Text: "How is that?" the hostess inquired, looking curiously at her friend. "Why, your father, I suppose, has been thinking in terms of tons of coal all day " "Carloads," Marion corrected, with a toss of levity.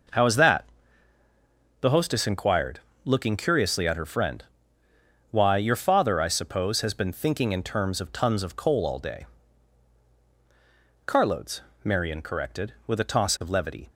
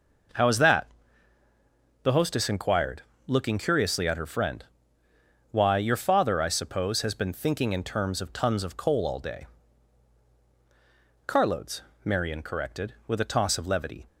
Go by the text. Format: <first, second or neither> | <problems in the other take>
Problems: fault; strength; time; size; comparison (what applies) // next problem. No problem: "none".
neither | none